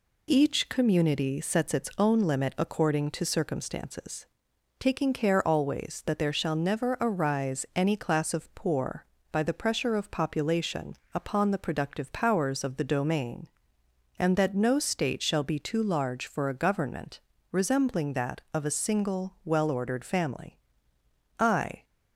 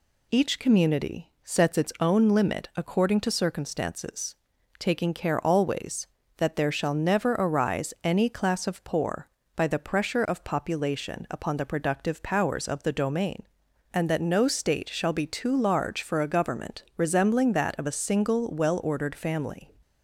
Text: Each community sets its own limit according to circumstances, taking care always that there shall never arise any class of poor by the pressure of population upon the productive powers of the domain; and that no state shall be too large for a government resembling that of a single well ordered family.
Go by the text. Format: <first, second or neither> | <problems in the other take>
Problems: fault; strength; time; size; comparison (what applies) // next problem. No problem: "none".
second | pauses between "population" and "upon"; slight; at 10.9 s; 0.18 s long // pauses between "government" and "resembling"; slight; at 17.2 s; 0.28 s long // goes on to say "I"; slight; from 21.3 s on; 0.44 s long